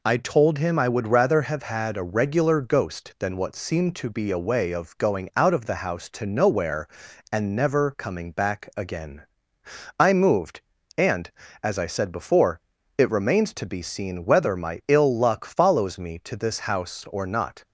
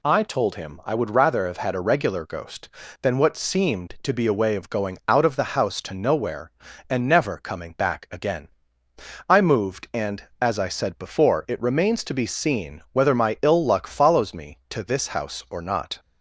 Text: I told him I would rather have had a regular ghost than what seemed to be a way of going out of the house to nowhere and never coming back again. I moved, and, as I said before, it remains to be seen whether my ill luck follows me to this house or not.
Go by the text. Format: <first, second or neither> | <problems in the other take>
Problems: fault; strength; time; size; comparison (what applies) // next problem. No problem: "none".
neither | none